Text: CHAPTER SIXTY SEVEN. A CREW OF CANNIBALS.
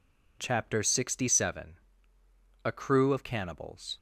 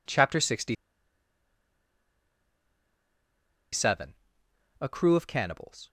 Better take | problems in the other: first | pauses between "SIXTY" and "SEVEN"; strong; at 0.7 s; 2.9 s long

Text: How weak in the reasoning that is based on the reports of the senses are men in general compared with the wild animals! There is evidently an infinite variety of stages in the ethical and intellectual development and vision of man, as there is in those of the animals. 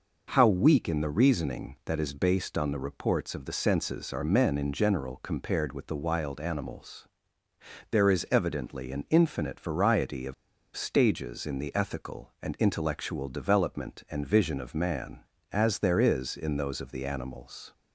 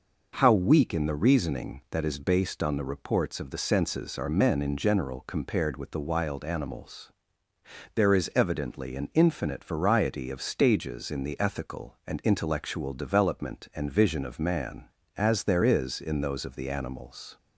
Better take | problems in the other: second | pauses between "of" and "stages"; at 10.3 s; 0.41 s long

